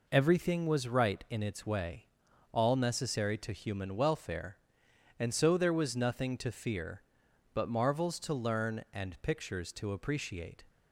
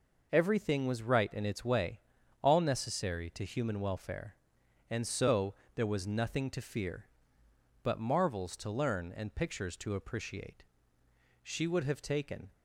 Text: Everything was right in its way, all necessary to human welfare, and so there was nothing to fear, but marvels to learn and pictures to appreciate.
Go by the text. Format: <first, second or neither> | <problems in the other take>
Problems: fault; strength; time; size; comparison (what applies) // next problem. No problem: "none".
first | pauses between "so" and "there"; slight; at 5.5 s; 0.22 s long // goes on to say "She would have taken"; noticeable; from 11.4 s on; 1.0 s long